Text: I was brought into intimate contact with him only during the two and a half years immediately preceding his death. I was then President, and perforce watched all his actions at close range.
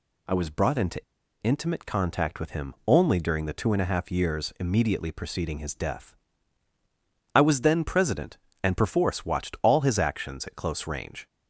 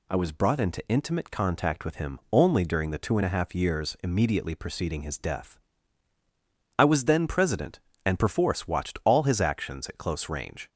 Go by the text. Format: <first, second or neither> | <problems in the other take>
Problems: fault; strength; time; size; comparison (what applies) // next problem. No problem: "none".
second | pauses between "into" and "intimate"; at 0.9 s; 0.43 s long